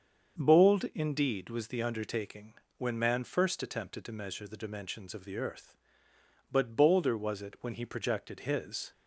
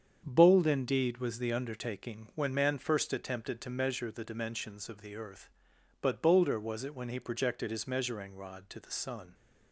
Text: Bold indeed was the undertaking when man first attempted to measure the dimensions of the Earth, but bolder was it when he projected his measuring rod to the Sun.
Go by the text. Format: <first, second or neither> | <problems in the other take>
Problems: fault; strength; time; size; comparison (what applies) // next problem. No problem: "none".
second | starts louder than the rest; until 1.4 s; 7 dB; strong in the second // pauses between "undertaking" and "when"; slight; at 2.5 s; 0.24 s long // stops before "measuring rod to the Sun"; at 8.9 s